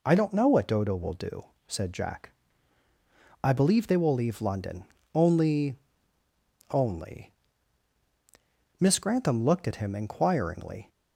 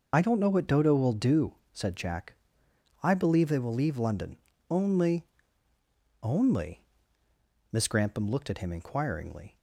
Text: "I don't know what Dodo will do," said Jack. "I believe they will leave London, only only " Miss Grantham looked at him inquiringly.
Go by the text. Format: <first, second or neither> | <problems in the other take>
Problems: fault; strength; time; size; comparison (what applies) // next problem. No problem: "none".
first | loses the start of "I"; at 0.1 s; 40 ms // starts louder than the rest; noticeable; until 1.1 s; 6 dB // pauses between "only" and "only"; noticeable; at 5.2 s; 0.96 s long; noticeable in the first